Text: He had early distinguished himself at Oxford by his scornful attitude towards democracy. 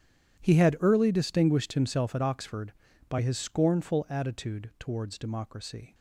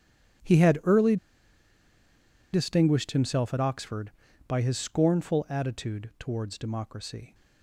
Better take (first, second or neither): first